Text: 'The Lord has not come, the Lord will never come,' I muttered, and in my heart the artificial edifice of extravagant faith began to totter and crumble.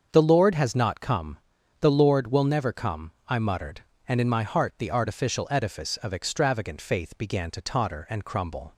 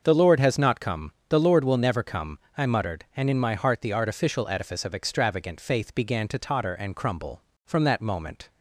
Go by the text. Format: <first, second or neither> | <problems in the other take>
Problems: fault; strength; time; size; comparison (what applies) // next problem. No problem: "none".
first | starts louder than the rest; until 1.0 s; 6.5 dB; also in the first // goes on to say "From that moment"; noticeable; from 7.6 s on; 0.84 s long